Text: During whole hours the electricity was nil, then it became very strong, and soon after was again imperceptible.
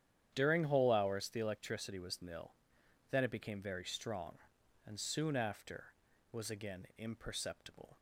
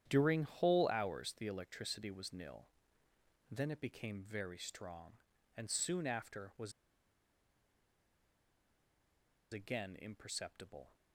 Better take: first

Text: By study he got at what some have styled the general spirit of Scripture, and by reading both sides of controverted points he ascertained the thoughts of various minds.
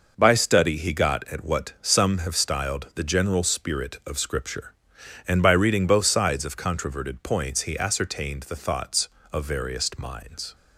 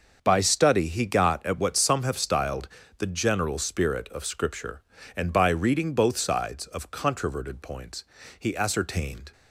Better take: first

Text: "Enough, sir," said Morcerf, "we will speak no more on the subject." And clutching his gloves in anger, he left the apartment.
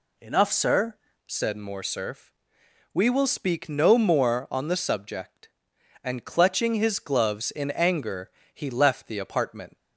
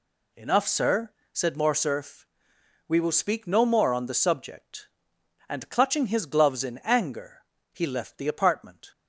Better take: second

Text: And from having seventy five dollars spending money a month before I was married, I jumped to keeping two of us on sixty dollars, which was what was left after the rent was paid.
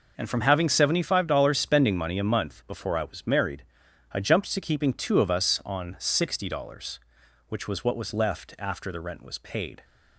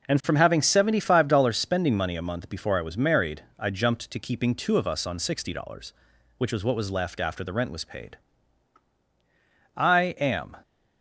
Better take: first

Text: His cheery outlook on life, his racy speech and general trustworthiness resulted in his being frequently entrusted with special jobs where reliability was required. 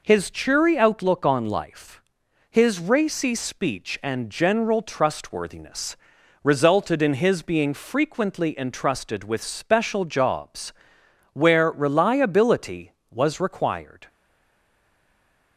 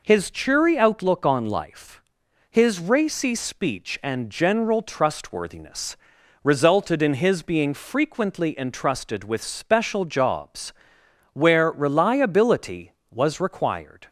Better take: second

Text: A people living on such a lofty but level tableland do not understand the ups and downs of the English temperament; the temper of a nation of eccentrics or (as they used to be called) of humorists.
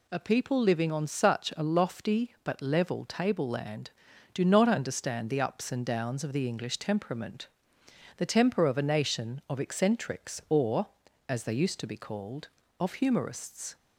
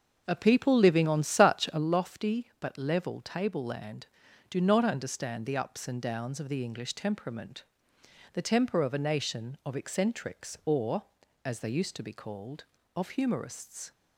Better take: first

